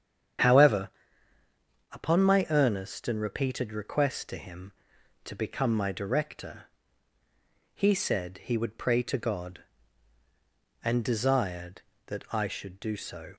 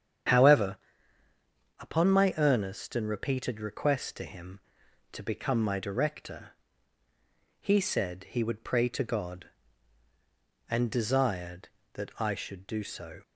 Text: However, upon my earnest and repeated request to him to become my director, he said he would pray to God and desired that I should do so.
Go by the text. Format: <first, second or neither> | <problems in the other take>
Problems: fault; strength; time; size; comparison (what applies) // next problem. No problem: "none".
neither | starts louder than the rest; strong; the same in both